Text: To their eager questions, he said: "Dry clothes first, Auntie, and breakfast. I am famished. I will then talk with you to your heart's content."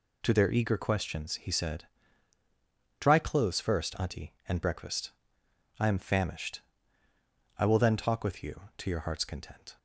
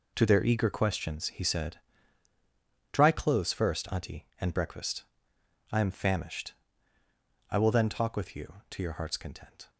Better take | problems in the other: first | gets quieter; strong; throughout; 10.5 dB

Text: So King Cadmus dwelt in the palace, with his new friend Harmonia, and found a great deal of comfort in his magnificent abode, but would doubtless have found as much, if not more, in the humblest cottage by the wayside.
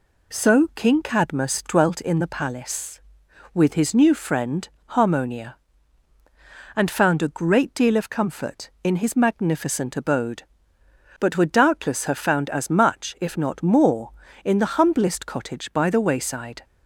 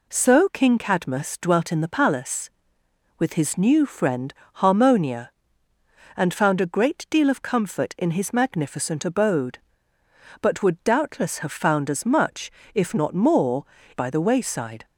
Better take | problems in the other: first | pauses between "friend" and "Harmonia"; slight; at 4.3 s; 0.22 s long; slight in the first // skips "in the humblest cottage"; at 13.8 s

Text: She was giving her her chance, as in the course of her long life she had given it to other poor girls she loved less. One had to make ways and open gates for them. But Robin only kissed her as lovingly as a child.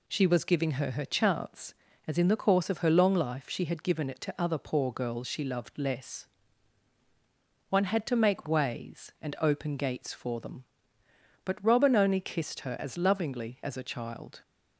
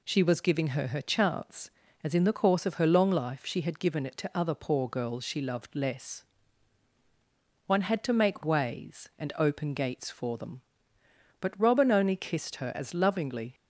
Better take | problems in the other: first | stops before "as a child"; at 13.5 s

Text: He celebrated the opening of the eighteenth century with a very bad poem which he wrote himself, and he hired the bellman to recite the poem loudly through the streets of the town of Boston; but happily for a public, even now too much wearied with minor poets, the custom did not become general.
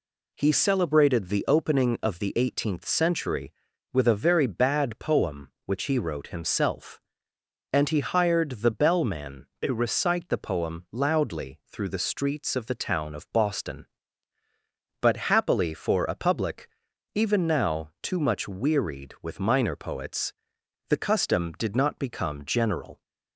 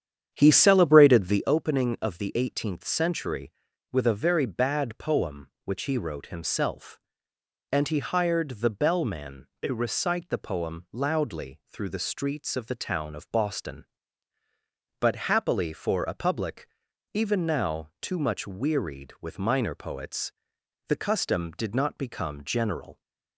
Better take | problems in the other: first | starts louder than the rest; strong; until 1.5 s; 9 dB

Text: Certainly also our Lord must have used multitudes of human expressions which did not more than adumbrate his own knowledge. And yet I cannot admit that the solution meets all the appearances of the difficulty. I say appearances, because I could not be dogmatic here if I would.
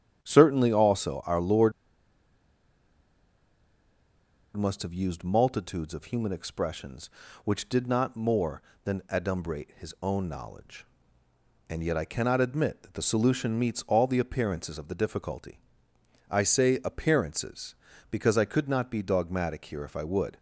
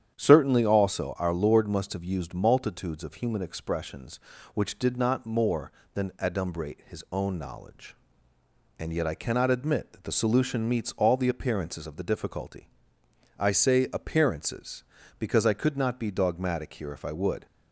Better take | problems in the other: second | starts louder than the rest; strong; until 1.2 s; 9 dB; strong in the second // pauses between "Lord" and "must"; strong; at 1.7 s; 2.8 s long

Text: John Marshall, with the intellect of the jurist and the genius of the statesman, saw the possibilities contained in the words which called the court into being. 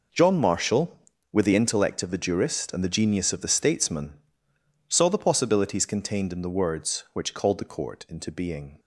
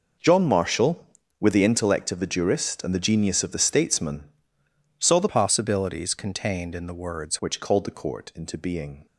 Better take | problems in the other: first | changes voice from "possibilities" to "words"; from 5.2 to 7.3 s; 2.1 s long

